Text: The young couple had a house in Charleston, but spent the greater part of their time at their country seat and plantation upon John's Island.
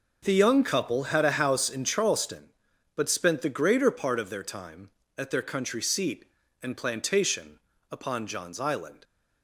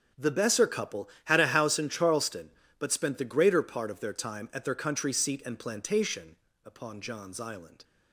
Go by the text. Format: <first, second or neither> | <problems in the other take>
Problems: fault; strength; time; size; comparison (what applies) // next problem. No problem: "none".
first | says "besser" for "young"; at 0.3 s // pauses between "plantation" and "upon"; slight; at 6.3 s; 0.28 s long; slight in the first